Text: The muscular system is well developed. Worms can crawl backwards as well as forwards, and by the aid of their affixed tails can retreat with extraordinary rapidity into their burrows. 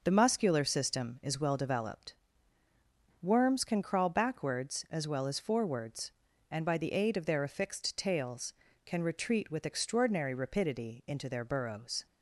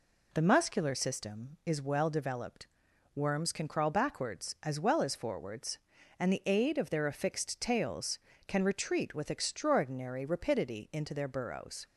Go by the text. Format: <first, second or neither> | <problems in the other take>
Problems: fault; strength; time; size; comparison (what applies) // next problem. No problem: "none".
first | skips "by"; at 6.3 s